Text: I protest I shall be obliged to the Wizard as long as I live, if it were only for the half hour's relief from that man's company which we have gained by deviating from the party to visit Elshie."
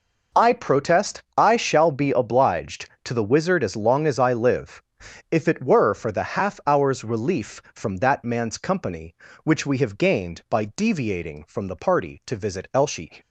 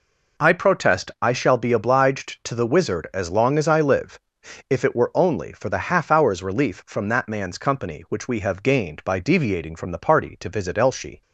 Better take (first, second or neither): second